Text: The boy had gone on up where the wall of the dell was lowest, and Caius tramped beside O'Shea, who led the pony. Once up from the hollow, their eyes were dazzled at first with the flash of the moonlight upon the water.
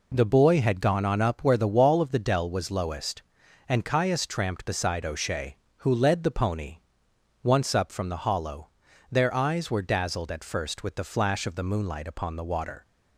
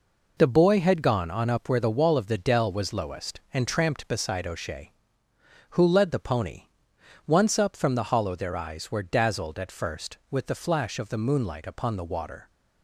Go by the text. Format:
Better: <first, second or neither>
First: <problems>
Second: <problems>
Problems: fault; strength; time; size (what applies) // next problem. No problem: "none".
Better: first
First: none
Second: skips "Caius"; at 3.6 s